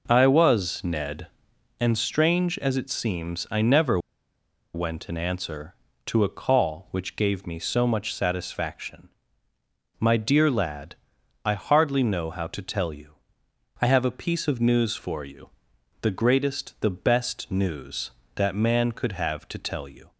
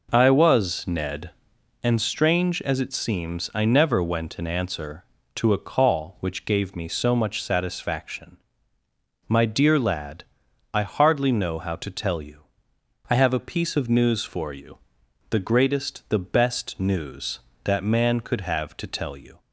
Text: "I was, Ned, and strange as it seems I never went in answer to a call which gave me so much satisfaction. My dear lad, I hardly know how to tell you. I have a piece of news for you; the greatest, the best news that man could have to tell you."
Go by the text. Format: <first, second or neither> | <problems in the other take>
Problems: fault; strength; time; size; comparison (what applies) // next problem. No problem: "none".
second | pauses between "never" and "went"; noticeable; at 3.9 s; 0.76 s long